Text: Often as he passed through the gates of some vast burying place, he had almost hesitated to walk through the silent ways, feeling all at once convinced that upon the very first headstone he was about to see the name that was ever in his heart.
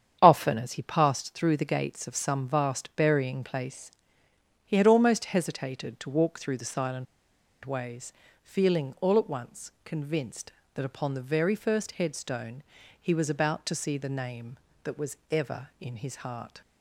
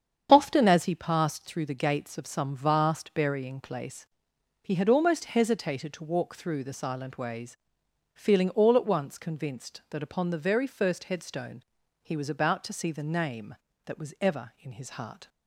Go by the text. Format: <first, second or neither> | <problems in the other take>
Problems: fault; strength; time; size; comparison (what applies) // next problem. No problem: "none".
second | starts louder than the rest; strong; until 1.2 s; 8.5 dB; strong in the second // pauses between "silent" and "ways"; noticeable; at 7.0 s; 0.59 s long // pauses between "headstone" and "he"; at 12.6 s; 0.40 s long; also in the second // pauses between "was" and "ever"; slight; at 15.1 s; 0.16 s long